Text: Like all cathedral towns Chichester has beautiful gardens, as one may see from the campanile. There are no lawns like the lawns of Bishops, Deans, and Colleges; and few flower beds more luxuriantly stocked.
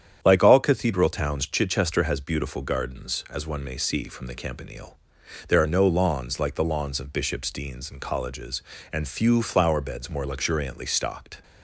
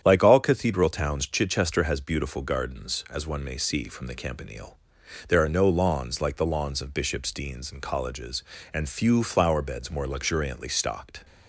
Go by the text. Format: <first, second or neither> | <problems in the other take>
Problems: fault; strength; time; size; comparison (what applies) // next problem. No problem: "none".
neither | starts louder than the rest; strong; the same in both